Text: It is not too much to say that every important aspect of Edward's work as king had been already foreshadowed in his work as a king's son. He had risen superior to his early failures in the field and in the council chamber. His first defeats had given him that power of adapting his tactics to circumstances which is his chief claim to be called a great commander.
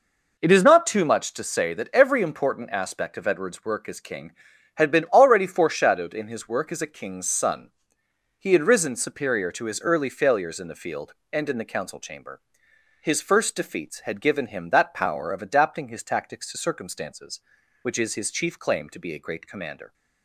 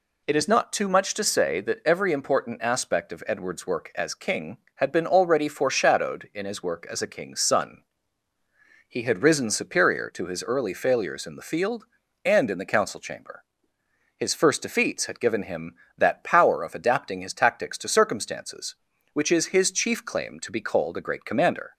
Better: second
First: skips "called"; at 19.1 s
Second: none

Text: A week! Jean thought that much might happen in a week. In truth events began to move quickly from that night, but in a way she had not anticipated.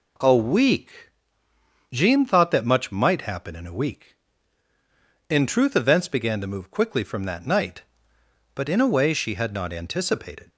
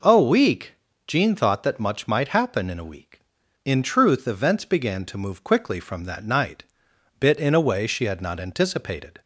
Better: first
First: none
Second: says "bit" for "but"; at 7.1 s

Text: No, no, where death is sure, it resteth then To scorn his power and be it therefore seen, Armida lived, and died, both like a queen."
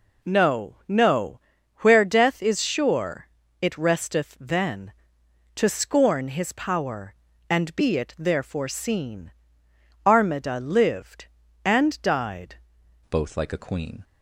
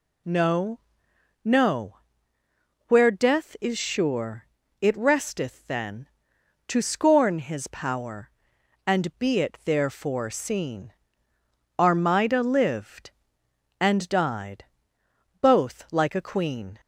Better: second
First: changes voice at "both"; from 13.1 s on; 0.9 s long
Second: none

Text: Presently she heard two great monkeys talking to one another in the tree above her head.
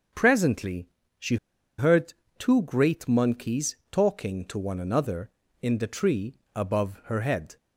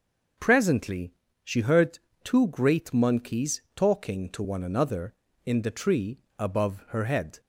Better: second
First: starts louder than the rest; until 1.8 s; 6.5 dB // pauses between "Presently" and "she"; slight; at 0.8 s; 0.32 s long // pauses between "she" and "heard"; at 1.3 s; 0.41 s long // pauses between "heard" and "two"; slight; at 2.1 s; 0.24 s long // pauses between "tree" and "above"; slight; at 6.3 s; 0.20 s long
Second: pauses between "Presently" and "she"; slight; at 1.1 s; 0.32 s long // pauses between "heard" and "two"; slight; at 1.9 s; 0.24 s long // pauses between "tree" and "above"; slight; at 6.1 s; 0.20 s long

